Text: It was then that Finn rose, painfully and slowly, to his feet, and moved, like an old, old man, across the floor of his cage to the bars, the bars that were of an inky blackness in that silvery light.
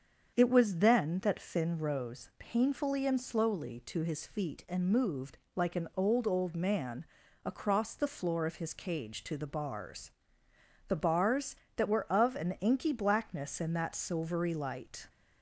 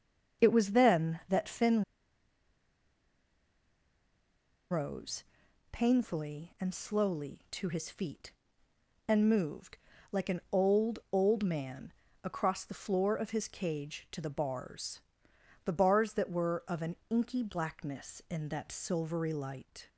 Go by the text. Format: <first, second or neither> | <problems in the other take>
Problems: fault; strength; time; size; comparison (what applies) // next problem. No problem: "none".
first | starts louder than the rest; until 1.5 s; 6.5 dB; strong in the first // pauses between "Finn" and "rose"; strong; at 1.8 s; 2.8 s long // pauses between "an" and "inky"; slight; at 16.9 s; 0.16 s long